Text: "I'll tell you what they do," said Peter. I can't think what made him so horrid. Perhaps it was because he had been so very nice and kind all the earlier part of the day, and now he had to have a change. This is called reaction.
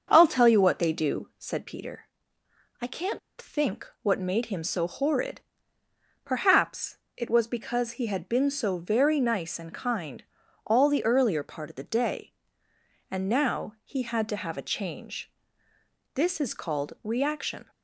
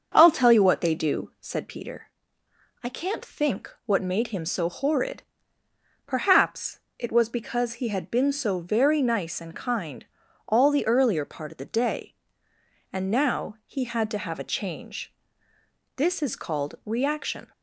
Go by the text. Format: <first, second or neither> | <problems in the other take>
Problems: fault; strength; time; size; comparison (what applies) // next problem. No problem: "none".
second | starts louder than the rest; until 1.1 s; 6.5 dB; also in the second // pauses between "can't" and "think"; slight; at 3.1 s; 0.20 s long // pauses between "Perhaps" and "it"; slight; at 6.9 s; 0.18 s long; slight in the second // pauses between "kind" and "all"; at 10.2 s; 0.42 s long; also in the second